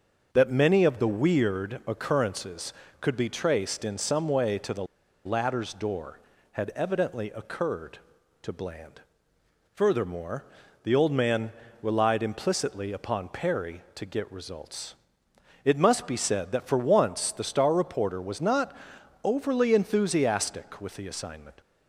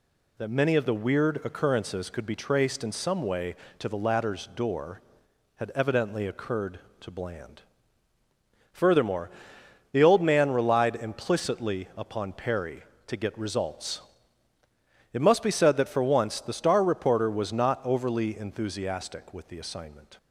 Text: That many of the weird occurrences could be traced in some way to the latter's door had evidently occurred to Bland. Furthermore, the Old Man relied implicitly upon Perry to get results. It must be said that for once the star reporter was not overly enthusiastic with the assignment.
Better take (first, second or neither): second